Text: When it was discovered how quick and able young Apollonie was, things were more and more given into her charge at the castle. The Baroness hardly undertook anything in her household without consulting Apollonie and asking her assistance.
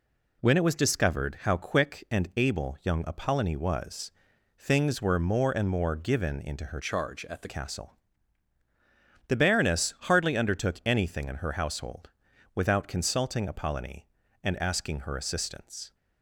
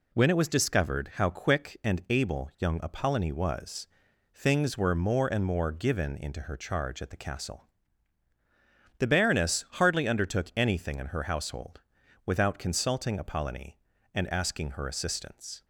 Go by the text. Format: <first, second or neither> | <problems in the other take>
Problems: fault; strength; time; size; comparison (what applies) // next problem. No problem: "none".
second | changes voice from "charge" to "the"; from 6.8 to 7.4 s; 0.6 s long // pauses between "household" and "without"; at 12.0 s; 0.44 s long; also in the second